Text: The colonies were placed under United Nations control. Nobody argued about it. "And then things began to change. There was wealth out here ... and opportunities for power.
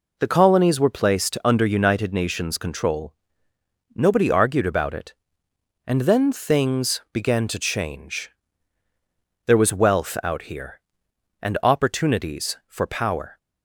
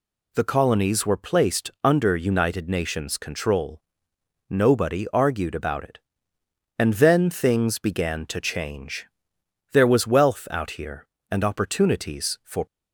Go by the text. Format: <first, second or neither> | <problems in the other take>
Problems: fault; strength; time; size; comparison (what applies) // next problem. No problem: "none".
first | stops before "power"; at 12.6 s